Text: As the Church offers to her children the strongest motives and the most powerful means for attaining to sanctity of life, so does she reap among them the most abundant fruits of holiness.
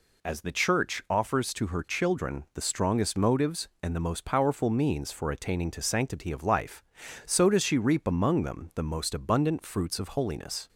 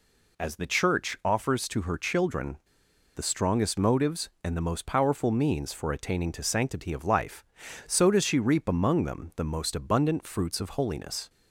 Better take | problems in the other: first | pauses between "children" and "the"; noticeable; at 2.5 s; 0.59 s long

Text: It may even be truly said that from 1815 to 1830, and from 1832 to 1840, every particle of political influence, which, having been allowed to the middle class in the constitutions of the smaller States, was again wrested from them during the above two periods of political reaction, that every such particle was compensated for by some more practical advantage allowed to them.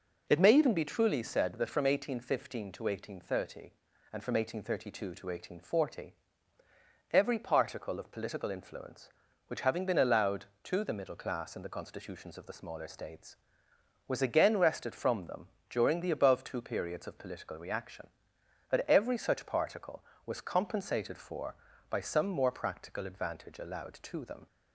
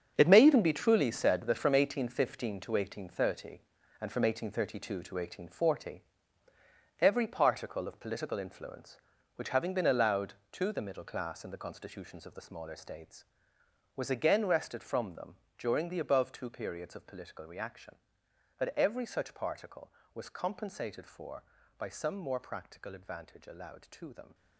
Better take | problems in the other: first | gets quieter; strong; throughout; 11.5 dB // pauses between "them" and "during"; slight; at 15.3 s; 0.20 s long; slight in the first

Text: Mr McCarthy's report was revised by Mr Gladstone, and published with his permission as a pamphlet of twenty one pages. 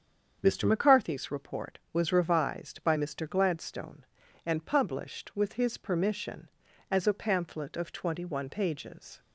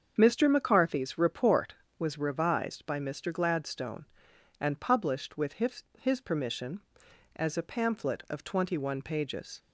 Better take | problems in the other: first | starts louder than the rest; until 1.1 s; 7 dB; strong in the first // says "his" twice; at 5.9 s

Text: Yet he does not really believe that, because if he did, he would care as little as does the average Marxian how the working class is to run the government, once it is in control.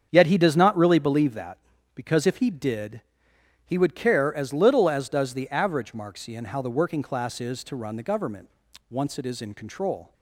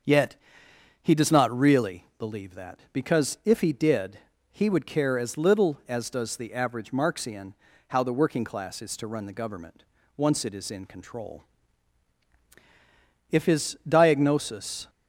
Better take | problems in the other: first | starts louder than the rest; until 1.7 s; 7 dB; strong in the first // pauses between "Yet" and "he"; noticeable; at 0.3 s; 0.66 s long // pauses between "Marxian" and "how"; slight; at 7.5 s; 0.34 s long // goes on to say "If his diagnosis"; from 13.3 s on; 1.5 s long

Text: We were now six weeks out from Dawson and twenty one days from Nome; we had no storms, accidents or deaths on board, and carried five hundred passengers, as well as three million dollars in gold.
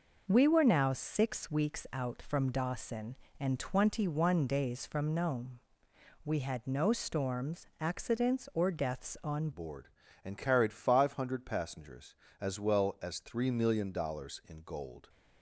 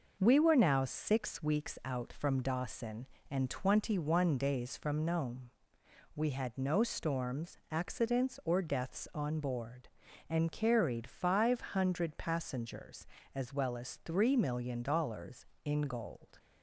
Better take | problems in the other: second | changes voice at "board"; from 9.5 s on; 5.5 s long

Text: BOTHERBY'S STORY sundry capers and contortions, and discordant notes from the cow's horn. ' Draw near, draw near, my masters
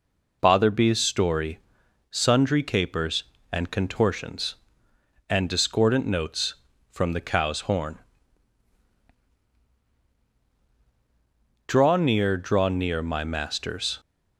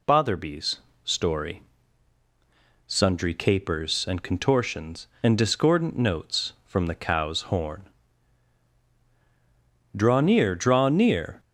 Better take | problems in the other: first | pauses between "BOTHERBY'S" and "STORY"; slight; at 0.7 s; 0.26 s long // pauses between "STORY" and "sundry"; at 1.6 s; 1.2 s long; noticeable in the first // stops before "my masters"; at 11.3 s

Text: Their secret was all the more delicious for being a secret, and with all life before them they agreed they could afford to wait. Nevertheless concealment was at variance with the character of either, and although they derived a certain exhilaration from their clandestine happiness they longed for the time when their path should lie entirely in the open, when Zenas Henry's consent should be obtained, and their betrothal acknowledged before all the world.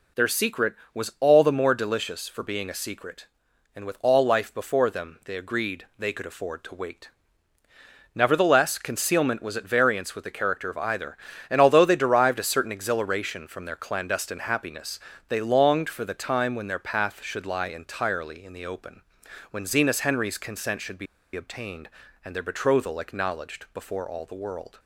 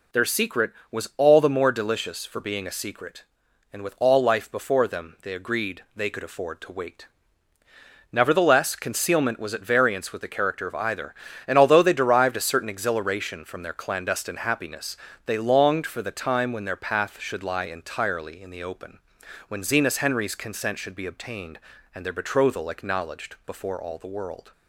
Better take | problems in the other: second | pauses between "happiness" and "they"; slight; at 14.9 s; 0.30 s long; slight in the second // pauses between "be" and "obtained"; slight; at 21.0 s; 0.29 s long

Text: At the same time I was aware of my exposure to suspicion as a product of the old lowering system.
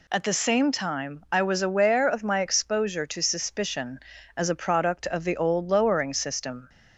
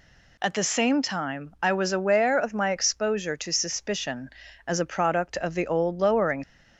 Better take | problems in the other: first | stops before "system"; at 6.4 s

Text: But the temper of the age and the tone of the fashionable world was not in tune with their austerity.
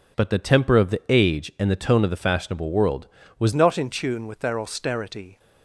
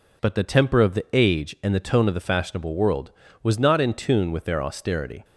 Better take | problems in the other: second | changes voice at "not"; from 3.5 s on; 1.8 s long

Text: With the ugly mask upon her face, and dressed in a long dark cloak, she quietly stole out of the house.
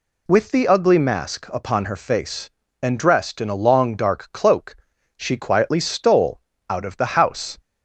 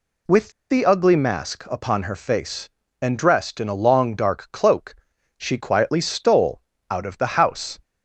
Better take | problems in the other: first | pauses between "With" and "the"; slight; at 0.4 s; 0.20 s long // pauses between "stole" and "out"; slight; at 6.5 s; 0.30 s long; slight in the first

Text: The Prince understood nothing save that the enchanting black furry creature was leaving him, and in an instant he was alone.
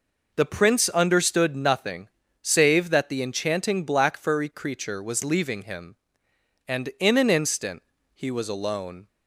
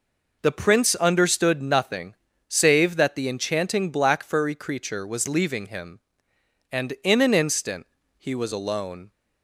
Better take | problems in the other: neither | pauses between "nothing" and "save"; slight; the same in both // pauses between "instant" and "he"; slight; the same in both

